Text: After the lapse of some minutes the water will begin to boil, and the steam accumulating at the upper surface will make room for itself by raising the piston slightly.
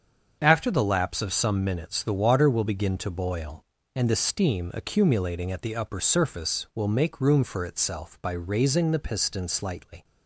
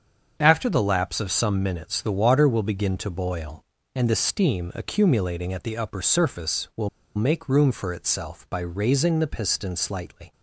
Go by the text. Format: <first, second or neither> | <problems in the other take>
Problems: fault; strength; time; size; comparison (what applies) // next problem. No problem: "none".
first | starts louder than the rest; until 1.4 s; 7 dB; also in the first // pauses between "will" and "make"; slight; at 6.8 s; 0.26 s long